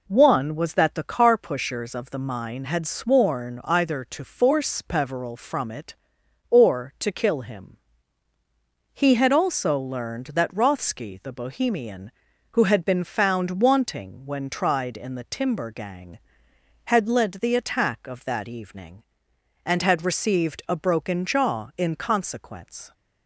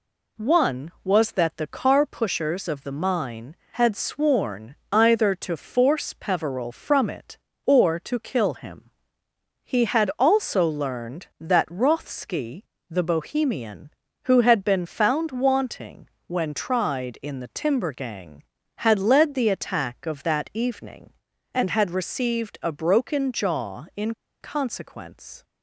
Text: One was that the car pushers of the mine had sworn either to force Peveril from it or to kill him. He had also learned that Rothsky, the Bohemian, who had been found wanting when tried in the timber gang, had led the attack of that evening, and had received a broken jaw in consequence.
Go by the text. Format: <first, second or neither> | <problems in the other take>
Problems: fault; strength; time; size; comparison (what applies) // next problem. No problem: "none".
first | pauses between "sworn" and "either"; slight; at 4.7 s; 0.16 s long // pauses between "wanting" and "when"; slight; at 16.0 s; 0.20 s long // pauses between "in" and "consequence"; slight; at 24.1 s; 0.27 s long